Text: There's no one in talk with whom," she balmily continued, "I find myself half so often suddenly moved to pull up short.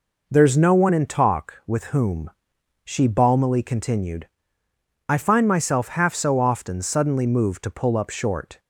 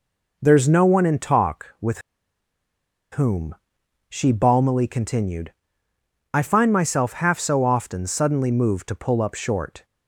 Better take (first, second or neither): first